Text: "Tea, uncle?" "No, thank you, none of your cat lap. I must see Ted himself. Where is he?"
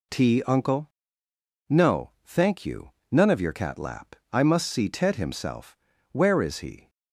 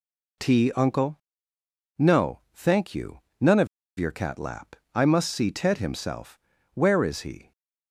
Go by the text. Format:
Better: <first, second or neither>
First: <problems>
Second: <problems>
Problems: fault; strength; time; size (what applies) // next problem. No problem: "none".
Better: first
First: none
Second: pauses between "of" and "your"; slight; at 3.6 s; 0.32 s long